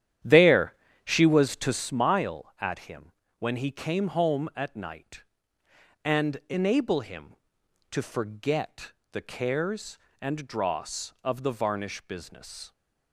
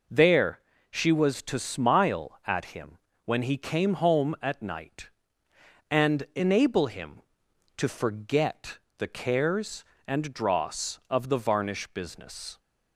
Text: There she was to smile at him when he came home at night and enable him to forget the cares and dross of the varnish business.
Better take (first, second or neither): second